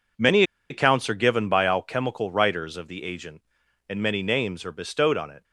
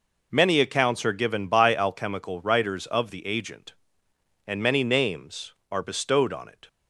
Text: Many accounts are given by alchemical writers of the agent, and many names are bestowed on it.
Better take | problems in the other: second | pauses between "Many" and "accounts"; slight; at 0.4 s; 0.27 s long

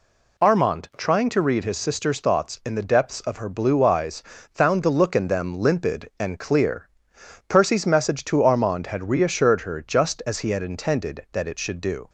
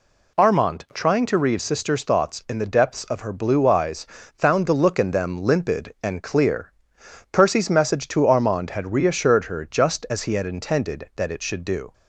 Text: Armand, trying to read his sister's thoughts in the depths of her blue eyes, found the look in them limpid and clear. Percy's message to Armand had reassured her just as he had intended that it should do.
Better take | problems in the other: first | skips "his"; at 1.6 s

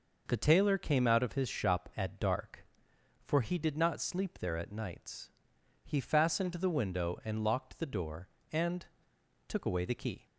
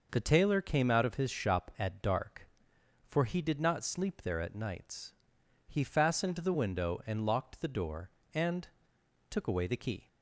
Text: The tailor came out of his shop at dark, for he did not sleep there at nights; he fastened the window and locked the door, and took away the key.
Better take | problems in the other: neither | pauses between "and" and "took"; noticeable; the same in both

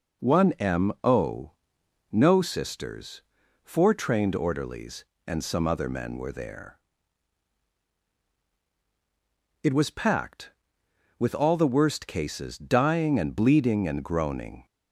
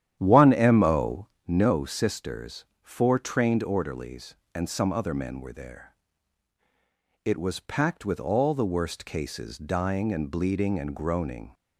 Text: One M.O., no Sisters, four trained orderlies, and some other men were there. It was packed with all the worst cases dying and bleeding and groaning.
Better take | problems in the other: first | starts louder than the rest; strong; until 1.4 s; 10.5 dB

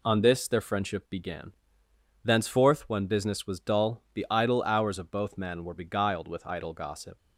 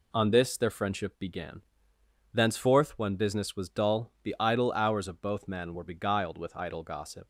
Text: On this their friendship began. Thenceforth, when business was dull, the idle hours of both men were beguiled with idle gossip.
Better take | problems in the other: neither | none

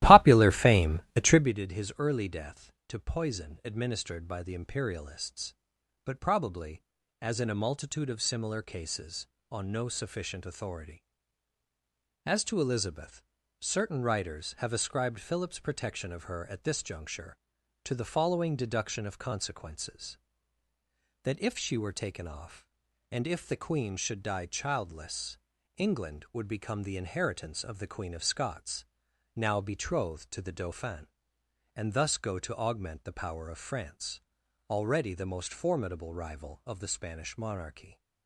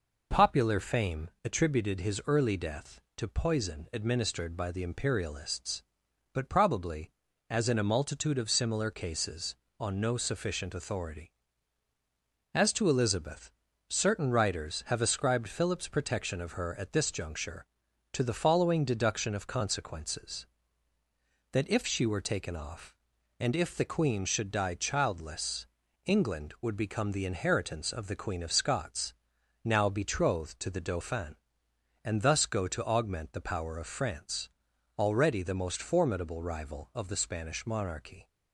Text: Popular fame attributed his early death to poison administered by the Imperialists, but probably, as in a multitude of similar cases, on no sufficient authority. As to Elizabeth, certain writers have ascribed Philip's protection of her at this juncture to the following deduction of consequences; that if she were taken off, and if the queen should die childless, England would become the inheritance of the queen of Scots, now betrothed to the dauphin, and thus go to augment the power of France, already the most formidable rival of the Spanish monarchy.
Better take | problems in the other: second | starts louder than the rest; strong; until 1.5 s; 16.5 dB // pauses between "fame" and "attributed"; slight; at 0.9 s; 0.16 s long; slight in the second

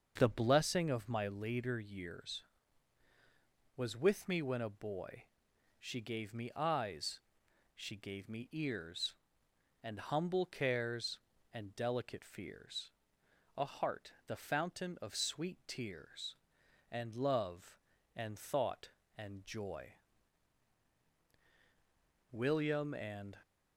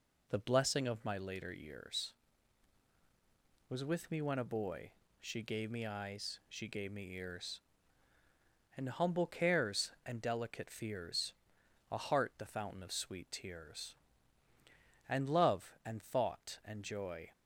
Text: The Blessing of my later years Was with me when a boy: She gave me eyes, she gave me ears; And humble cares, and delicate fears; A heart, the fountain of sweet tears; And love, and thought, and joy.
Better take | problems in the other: second | starts louder than the rest; until 1.1 s; 6.5 dB // goes on to say "William and"; noticeable; from 22.3 s on; 1.0 s long

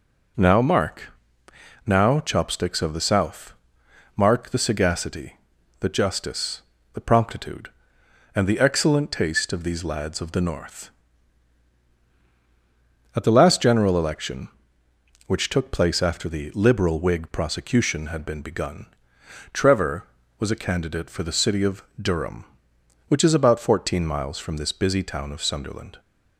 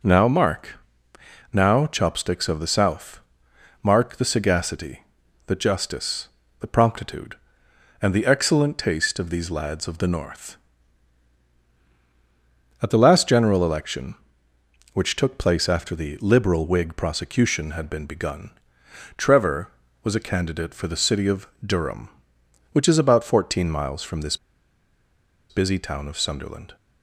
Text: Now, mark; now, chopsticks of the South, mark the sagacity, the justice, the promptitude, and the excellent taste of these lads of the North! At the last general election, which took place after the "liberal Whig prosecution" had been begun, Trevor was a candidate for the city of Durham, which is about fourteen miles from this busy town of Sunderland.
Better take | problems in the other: first | pauses between "of" and "Durham"; slight; at 21.4 s; 0.18 s long; slight in the first // pauses between "this" and "busy"; at 24.3 s; 1.1 s long

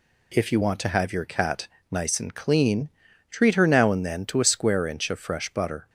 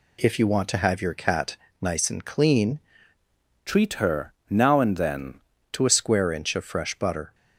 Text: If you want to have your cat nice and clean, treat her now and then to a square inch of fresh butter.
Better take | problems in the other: first | pauses between "cat" and "nice"; slight; at 1.5 s; 0.24 s long; slight in the first // changes voice from "treat" to "then"; from 3.6 to 5.3 s; 1.7 s long // pauses between "her" and "now"; slight; at 4.3 s; 0.16 s long

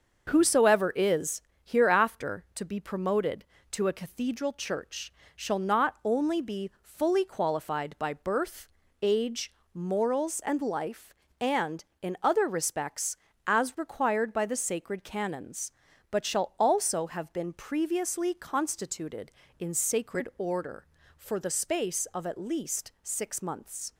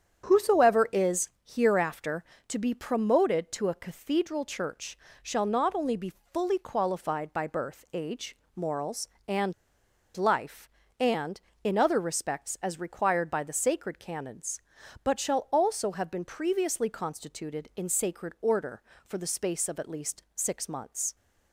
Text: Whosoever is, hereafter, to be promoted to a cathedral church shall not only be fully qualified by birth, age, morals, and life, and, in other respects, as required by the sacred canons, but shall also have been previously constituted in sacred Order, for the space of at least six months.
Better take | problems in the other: first | starts louder than the rest; strong; until 1.2 s; 7.5 dB; also in the first // pauses between "church" and "shall"; slight; at 4.9 s; 0.26 s long; slight in the first // pauses between "be" and "fully"; slight; at 6.1 s; 0.20 s long // pauses between "and" and "life"; noticeable; at 9.5 s; 0.61 s long

